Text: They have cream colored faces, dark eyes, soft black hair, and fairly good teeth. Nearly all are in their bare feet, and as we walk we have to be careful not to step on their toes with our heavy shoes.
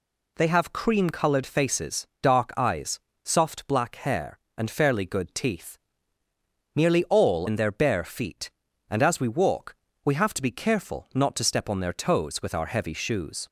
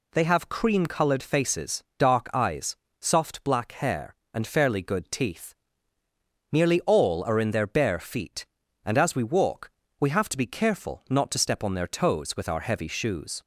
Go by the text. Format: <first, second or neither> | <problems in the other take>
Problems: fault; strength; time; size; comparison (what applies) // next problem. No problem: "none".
second | skips "are"; at 7.4 s // pauses between "walk" and "we"; slight; at 9.7 s; 0.30 s long; slight in the second